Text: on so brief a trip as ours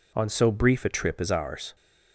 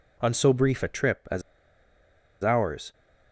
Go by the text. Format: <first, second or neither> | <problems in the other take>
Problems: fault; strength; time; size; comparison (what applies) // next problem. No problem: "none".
first | pauses between "as" and "ours"; at 1.4 s; 1.0 s long